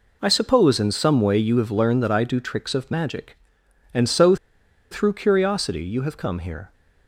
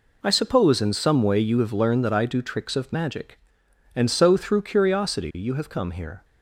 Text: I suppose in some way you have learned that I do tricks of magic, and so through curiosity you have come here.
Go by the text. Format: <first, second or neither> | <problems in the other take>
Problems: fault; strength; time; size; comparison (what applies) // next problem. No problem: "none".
second | pauses between "so" and "through"; noticeable; at 4.3 s; 0.55 s long